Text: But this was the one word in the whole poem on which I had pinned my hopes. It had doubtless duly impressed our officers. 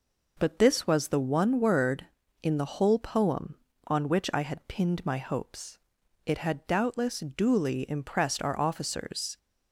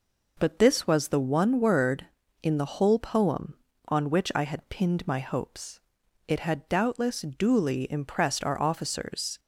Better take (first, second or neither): neither